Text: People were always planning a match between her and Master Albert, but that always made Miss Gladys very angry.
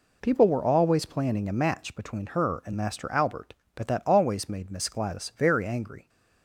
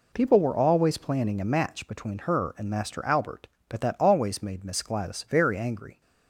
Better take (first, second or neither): neither